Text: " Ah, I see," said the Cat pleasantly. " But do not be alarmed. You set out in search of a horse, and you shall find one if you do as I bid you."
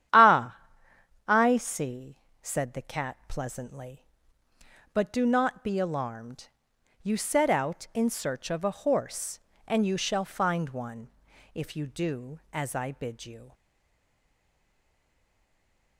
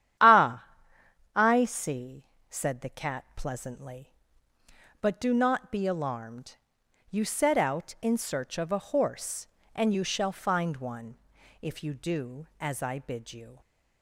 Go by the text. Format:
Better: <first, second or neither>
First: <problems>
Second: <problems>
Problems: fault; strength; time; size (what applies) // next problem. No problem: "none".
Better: second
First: starts louder than the rest; strong; until 1.8 s; 10.5 dB // pauses between "one" and "if"; at 11.1 s; 0.42 s long // stays silent after the last word; from 13.5 s on; 2.4 s long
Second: starts louder than the rest; strong; until 1.9 s; 10.5 dB // pauses between "one" and "if"; at 11.1 s; 0.42 s long